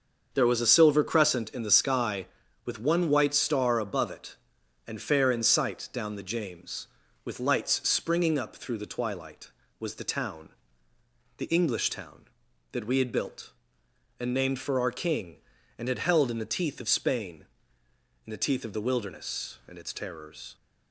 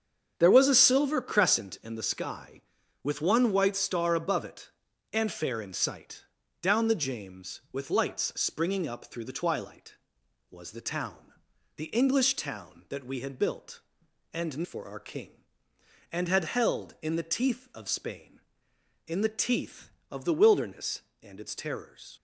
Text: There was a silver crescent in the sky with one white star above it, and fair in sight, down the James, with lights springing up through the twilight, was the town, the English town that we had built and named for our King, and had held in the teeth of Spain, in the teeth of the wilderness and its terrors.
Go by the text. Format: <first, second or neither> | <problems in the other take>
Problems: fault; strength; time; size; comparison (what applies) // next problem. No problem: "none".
first | starts louder than the rest; strong; until 1.3 s; 7.5 dB; also in the first // skips "named"; at 14.6 s